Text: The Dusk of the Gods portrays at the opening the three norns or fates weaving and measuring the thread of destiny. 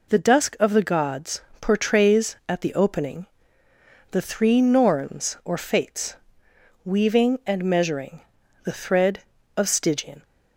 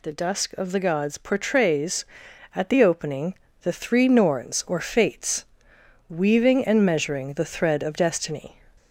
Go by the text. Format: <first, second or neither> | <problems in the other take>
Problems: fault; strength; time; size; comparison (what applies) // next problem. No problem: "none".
second | pauses between "Gods" and "portrays"; slight; at 1.4 s; 0.20 s long // pauses between "opening" and "the"; noticeable; at 3.2 s; 0.82 s long; slight in the second // pauses between "fates" and "weaving"; noticeable; at 6.1 s; 0.68 s long; noticeable in the second // pauses between "measuring" and "the"; at 8.2 s; 0.42 s long // says "stygian" for "destiny"; at 9.6 s